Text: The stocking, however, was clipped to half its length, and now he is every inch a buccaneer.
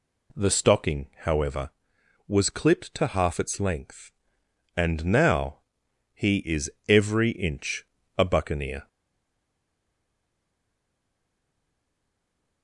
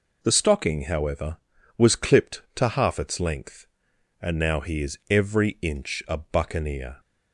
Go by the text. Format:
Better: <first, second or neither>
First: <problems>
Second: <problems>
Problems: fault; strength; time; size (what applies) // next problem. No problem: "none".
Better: second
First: pauses between "now" and "he"; noticeable; at 5.5 s; 0.54 s long // pauses between "is" and "every"; slight; at 6.6 s; 0.18 s long // pauses between "inch" and "a"; slight; at 7.8 s; 0.32 s long // stays silent after the last word; strong; from 8.8 s on; 3.8 s long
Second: none